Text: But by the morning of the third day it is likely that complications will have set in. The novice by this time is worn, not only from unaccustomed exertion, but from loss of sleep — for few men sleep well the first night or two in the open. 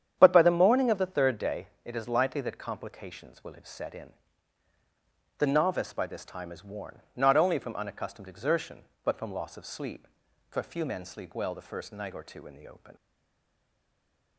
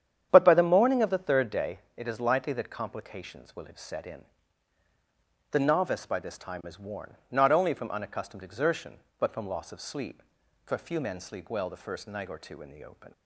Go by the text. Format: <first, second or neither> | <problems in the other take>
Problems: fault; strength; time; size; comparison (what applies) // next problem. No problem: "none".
second | starts louder than the rest; strong; until 1.2 s; 9 dB; strong in the second // pauses between "day" and "it"; slight; at 1.6 s; 0.16 s long; slight in the second // stays silent after the last word; noticeable; from 12.9 s on; 1.4 s long